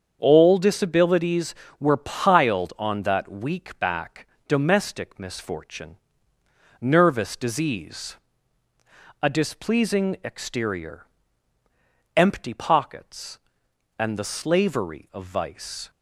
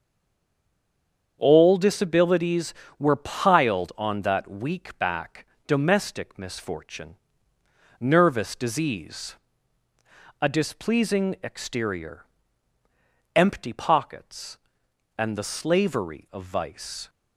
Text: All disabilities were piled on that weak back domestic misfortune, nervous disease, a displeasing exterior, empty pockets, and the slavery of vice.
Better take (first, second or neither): first